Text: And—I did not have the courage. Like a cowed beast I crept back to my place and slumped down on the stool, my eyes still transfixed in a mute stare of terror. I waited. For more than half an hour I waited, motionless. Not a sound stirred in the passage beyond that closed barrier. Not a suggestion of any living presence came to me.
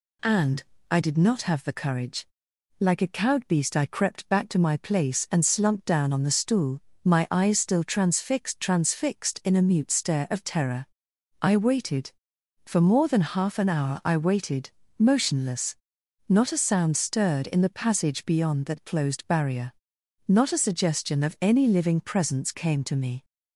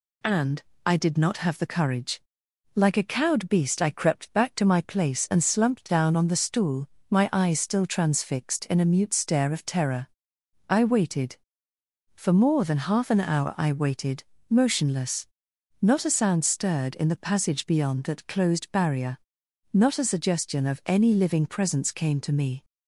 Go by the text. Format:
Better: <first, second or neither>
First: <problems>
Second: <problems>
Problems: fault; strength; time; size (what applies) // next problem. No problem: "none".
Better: second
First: says "transfixed" twice; at 8.5 s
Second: none